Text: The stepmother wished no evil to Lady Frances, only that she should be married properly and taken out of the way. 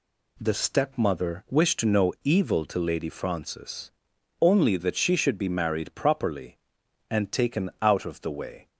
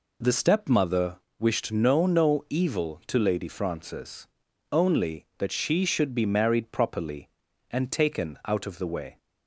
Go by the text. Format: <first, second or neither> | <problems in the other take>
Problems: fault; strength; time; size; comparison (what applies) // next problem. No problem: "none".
first | pauses between "stepmother" and "wished"; slight; at 1.1 s; 0.22 s long // says "no" twice; at 2.0 s